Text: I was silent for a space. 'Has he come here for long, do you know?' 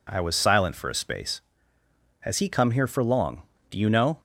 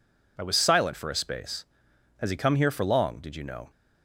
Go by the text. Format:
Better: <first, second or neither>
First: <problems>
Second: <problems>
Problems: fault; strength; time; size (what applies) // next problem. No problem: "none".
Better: first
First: none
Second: says "did" for "do"; at 3.1 s